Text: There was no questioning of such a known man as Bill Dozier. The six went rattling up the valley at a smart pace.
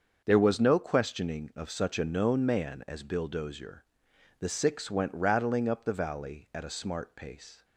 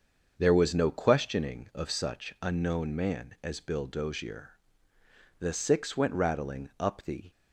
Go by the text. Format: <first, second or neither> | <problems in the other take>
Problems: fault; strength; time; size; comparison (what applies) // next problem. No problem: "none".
first | starts louder than the rest; until 1.3 s; 6.5 dB; also in the first // stops before "valley at a smart pace"; at 7.3 s